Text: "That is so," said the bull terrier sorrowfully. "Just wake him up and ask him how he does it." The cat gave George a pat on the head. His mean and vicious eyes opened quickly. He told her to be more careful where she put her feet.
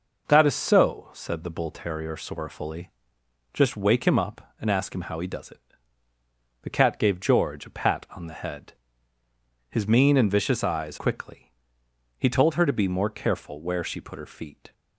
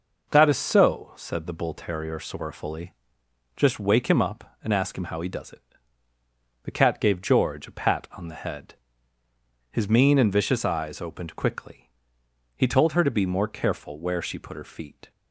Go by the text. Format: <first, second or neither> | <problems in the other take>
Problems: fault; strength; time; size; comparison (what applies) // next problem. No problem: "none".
second | skips "opened"; at 10.9 s